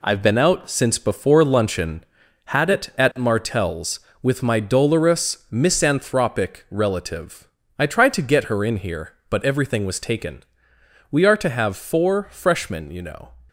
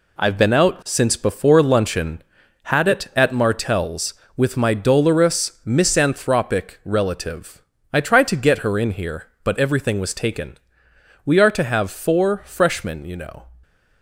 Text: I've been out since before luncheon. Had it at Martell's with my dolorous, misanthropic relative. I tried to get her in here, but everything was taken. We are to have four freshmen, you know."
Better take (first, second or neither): neither